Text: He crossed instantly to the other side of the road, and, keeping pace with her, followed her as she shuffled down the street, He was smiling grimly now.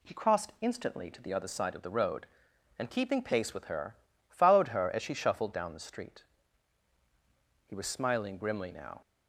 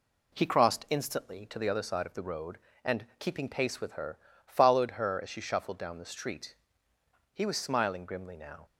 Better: neither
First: none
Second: none

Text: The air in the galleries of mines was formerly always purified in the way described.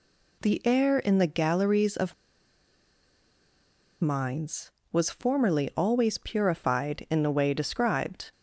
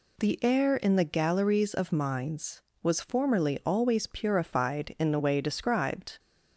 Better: second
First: pauses between "of" and "mines"; strong; at 2.1 s; 1.8 s long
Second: none

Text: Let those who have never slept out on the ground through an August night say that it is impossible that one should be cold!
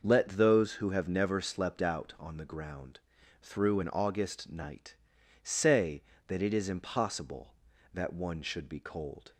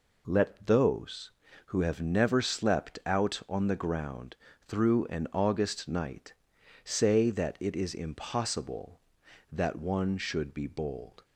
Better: first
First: pauses between "ground" and "through"; at 2.9 s; 0.42 s long // pauses between "night" and "say"; noticeable; at 4.9 s; 0.48 s long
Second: pauses between "ground" and "through"; slight; at 4.3 s; 0.32 s long // pauses between "night" and "say"; noticeable; at 6.3 s; 0.50 s long // says "bold" for "cold"; at 10.6 s

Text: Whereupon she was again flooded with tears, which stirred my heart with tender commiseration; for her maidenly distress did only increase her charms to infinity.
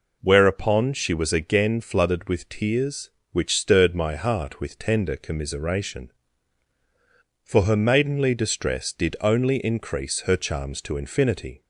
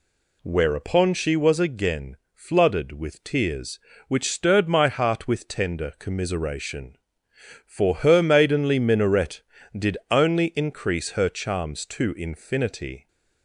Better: first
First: none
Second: pauses between "again" and "flooded"; slight; at 2.1 s; 0.16 s long // says "minaret" for "distress"; at 8.7 s

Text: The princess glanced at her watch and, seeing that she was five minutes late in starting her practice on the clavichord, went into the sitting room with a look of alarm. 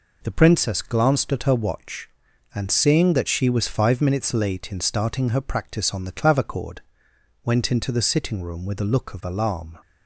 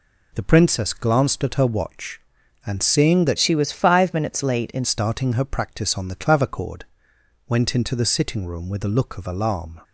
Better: first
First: none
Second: changes voice from "she" to "in"; from 3.3 to 4.8 s; 1.5 s long

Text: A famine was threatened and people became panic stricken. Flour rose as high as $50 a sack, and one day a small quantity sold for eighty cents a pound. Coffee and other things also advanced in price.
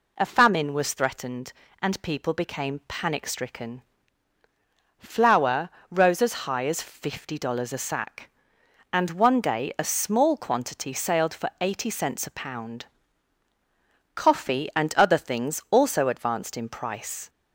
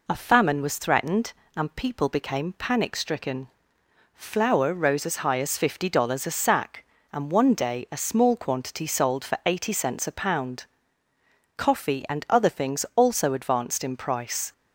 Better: second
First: pauses between "Flour" and "rose"; slight; at 5.6 s; 0.22 s long // says "sailed" for "sold"; at 10.9 s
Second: none

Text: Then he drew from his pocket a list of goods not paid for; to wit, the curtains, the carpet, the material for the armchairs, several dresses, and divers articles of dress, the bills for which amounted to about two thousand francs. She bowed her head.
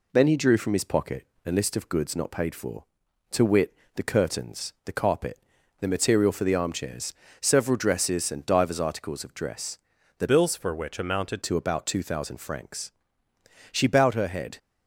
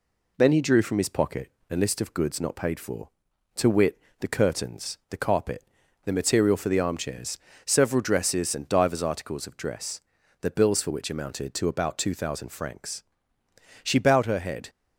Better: second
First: pauses between "pocket" and "a"; slight; at 1.2 s; 0.20 s long // changes voice from "bills" to "amounted"; from 10.2 to 11.4 s; 1.2 s long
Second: pauses between "pocket" and "a"; slight; at 1.5 s; 0.20 s long

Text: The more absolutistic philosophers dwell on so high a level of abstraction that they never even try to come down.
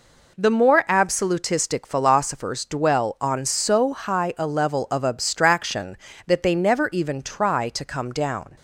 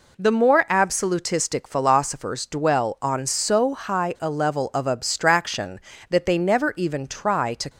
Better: first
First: none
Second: stops before "come down"; at 7.6 s

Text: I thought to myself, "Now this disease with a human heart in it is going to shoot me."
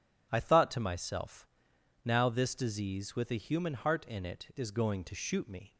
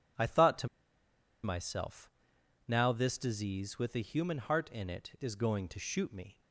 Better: first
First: none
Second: pauses between "to" and "myself"; noticeable; at 0.6 s; 0.76 s long

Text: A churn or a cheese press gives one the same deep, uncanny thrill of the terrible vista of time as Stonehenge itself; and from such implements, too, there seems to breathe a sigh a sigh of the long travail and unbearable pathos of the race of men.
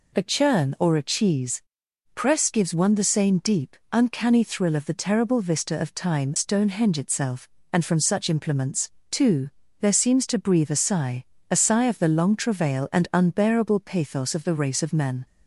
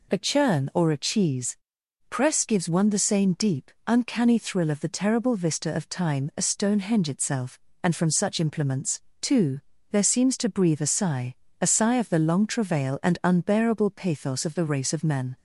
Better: second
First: pauses between "cheese" and "press"; noticeable; at 1.6 s; 0.50 s long // skips "as"; at 6.3 s // pauses between "sigh" and "a"; slight; at 11.2 s; 0.24 s long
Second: pauses between "cheese" and "press"; noticeable; at 1.5 s; 0.50 s long // pauses between "sigh" and "a"; slight; at 11.3 s; 0.24 s long

